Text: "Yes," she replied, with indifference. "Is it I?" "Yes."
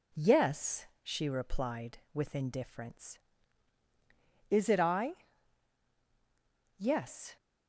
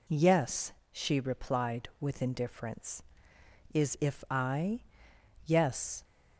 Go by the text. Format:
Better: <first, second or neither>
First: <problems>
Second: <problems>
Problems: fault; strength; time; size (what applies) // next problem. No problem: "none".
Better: first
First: none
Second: says "if" for "it"; at 3.9 s